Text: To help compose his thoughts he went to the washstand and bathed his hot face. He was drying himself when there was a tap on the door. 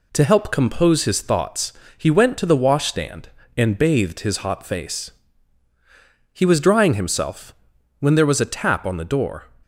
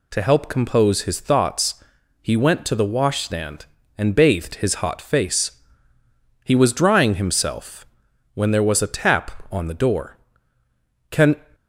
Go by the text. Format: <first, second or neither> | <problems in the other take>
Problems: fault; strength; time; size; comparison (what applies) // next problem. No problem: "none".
first | pauses between "thoughts" and "he"; at 1.8 s; 0.38 s long; slight in the first // pauses between "himself" and "when"; noticeable; at 7.8 s; 0.48 s long; noticeable in the first // goes on to say "Can"; slight; from 11.1 s on; 0.24 s long